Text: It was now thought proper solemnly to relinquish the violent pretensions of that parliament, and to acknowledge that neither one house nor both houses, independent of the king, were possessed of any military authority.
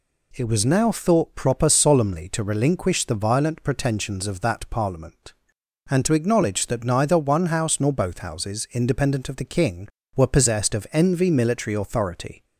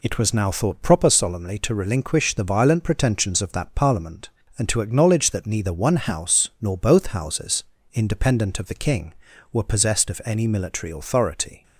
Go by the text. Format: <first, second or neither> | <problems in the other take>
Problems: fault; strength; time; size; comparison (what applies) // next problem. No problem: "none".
second | says "envy" for "any"; at 10.9 s